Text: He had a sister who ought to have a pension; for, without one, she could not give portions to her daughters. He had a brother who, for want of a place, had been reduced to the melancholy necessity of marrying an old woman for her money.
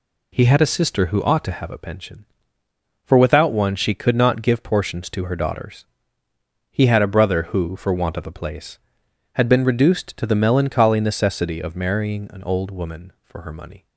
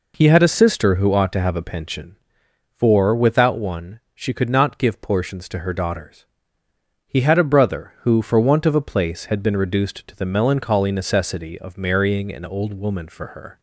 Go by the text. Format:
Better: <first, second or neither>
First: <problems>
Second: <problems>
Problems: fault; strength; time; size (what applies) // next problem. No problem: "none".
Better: first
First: none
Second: stops before "money"; at 13.5 s